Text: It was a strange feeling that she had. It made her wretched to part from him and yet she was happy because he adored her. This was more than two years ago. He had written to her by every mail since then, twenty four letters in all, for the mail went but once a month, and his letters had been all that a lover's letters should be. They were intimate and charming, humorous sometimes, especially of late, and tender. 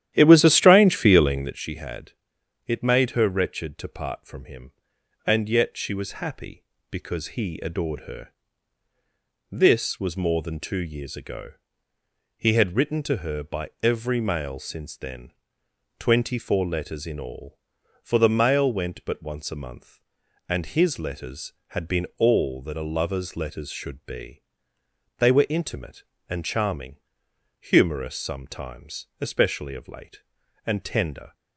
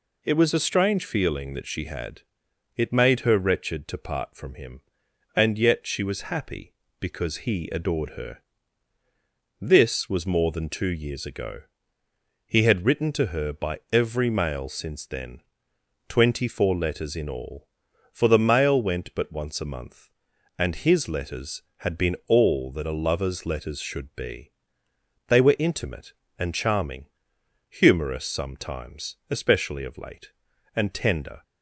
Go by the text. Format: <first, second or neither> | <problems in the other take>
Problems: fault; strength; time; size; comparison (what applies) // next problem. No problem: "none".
second | starts louder than the rest; strong; until 1.5 s; 11.5 dB